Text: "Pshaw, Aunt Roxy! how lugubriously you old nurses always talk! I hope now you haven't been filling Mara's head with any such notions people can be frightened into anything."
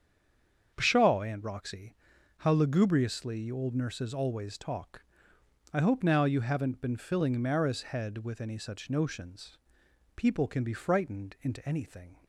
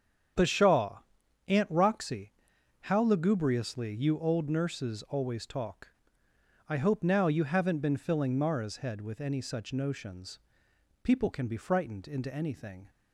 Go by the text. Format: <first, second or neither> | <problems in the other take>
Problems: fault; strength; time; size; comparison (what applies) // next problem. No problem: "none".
second | stays silent before the first word; slight; until 0.7 s; 0.7 s long // starts louder than the rest; strong; until 1.7 s; 7 dB; strong in the second // pauses between "notions" and "people"; noticeable; at 9.5 s; 0.58 s long; noticeable in the second